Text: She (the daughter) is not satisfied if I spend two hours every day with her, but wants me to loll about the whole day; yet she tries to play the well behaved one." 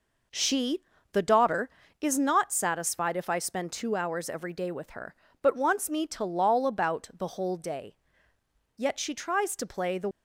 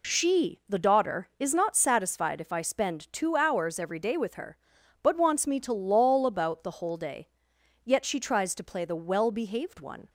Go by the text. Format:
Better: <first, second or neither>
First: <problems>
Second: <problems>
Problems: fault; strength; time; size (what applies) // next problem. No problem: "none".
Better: second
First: stops before "well behaved one"; at 10.1 s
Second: none